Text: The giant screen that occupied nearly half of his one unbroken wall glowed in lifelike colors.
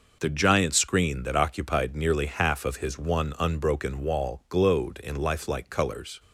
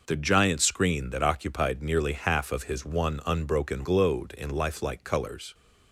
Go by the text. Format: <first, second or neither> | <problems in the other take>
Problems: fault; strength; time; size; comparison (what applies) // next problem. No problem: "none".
first | skips "wall"; at 3.8 s